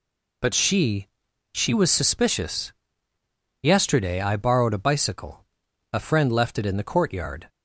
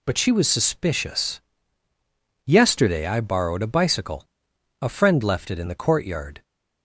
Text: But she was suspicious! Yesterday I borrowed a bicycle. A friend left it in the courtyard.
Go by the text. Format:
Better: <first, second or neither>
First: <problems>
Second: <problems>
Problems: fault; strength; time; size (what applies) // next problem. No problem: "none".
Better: second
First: says "she" twice; at 1.5 s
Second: none